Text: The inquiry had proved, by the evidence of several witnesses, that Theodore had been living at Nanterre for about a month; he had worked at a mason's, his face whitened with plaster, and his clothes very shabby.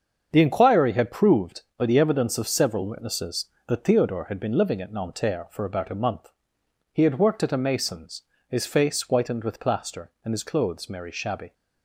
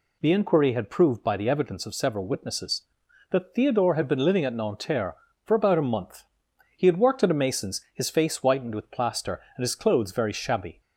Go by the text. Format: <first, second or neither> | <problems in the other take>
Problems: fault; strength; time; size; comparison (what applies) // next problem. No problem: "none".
second | starts louder than the rest; strong; until 1.3 s; 7 dB // says "merry" for "very"; at 10.8 s